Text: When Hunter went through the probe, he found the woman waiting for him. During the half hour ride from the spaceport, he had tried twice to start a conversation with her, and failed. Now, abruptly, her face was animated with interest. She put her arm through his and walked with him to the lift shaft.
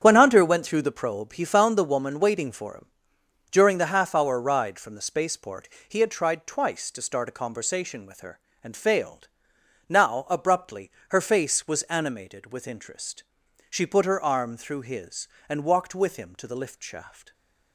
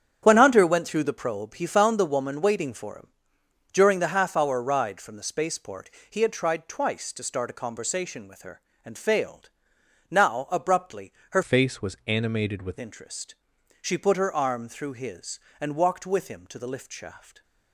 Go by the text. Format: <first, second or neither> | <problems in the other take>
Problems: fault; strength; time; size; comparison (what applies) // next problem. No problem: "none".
first | starts louder than the rest; strong; until 1.2 s; 9 dB; strong in the first // changes voice from "face" to "with"; from 11.4 to 12.7 s; 1.3 s long